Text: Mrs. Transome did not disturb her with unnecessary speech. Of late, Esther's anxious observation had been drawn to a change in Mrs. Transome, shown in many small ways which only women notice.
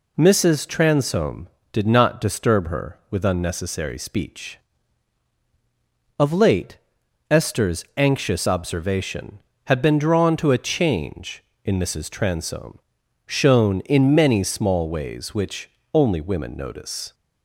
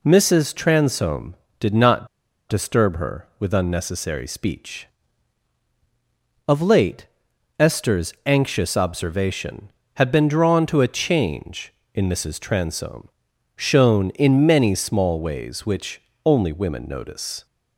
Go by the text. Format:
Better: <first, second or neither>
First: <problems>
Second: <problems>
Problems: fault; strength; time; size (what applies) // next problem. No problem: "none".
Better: first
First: pauses between "which" and "only"; slight; at 15.6 s; 0.24 s long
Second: pauses between "not" and "disturb"; at 2.0 s; 0.41 s long // pauses between "which" and "only"; slight; at 16.0 s; 0.24 s long